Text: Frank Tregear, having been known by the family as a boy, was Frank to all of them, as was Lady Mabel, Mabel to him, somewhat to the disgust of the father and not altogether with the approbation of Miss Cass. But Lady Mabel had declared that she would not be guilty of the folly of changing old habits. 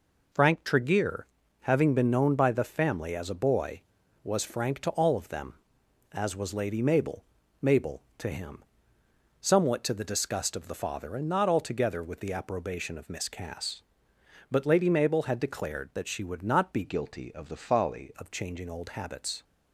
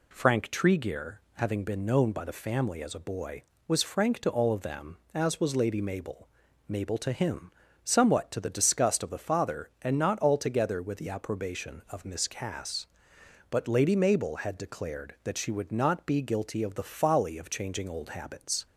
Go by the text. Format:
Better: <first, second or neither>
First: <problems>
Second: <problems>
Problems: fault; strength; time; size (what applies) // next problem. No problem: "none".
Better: second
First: changes voice from "guilty" to "folly"; from 16.8 to 18.1 s; 1.3 s long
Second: none